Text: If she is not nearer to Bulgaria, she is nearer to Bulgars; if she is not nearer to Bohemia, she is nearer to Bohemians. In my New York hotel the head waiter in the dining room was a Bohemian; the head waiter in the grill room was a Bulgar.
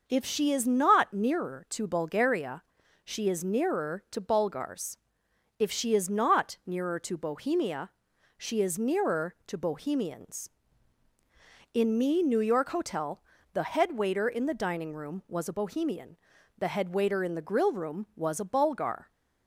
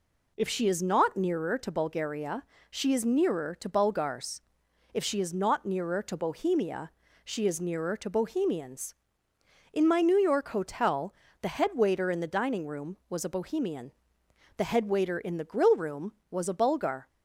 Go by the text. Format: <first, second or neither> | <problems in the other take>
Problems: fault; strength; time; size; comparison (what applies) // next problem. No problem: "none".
second | says "me" for "my"; at 11.9 s // pauses between "hotel" and "the"; slight; at 13.1 s; 0.34 s long; slight in the second